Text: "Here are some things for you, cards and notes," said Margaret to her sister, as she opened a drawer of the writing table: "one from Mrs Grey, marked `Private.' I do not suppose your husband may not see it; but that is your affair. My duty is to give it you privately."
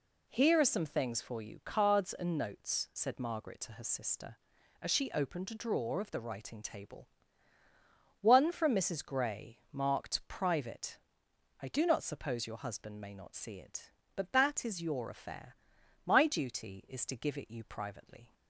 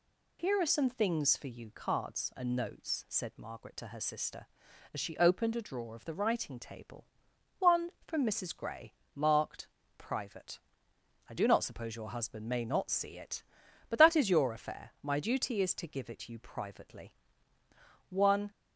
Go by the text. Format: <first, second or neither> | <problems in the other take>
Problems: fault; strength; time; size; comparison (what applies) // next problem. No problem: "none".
first | pauses between "marked" and "Private"; slight; at 9.6 s; 0.30 s long // goes on to say "One"; slight; from 18.0 s on; 0.42 s long